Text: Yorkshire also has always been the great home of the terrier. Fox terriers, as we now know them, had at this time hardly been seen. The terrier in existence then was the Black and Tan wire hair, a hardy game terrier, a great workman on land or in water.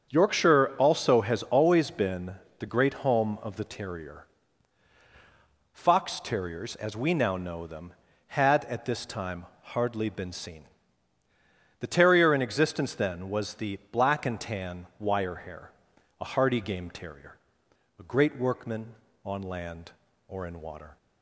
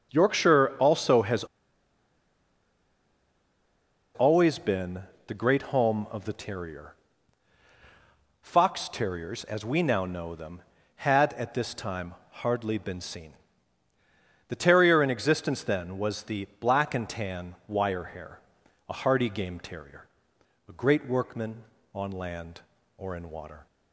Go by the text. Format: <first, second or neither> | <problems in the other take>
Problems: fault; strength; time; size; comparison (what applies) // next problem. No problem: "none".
first | starts louder than the rest; strong; until 1.1 s; 7 dB; strong in the first // pauses between "has" and "always"; strong; at 1.4 s; 2.7 s long // pauses between "been" and "the"; slight; at 5.0 s; 0.24 s long; slight in the first // pauses between "time" and "hardly"; slight; at 12.1 s; 0.18 s long; slight in the first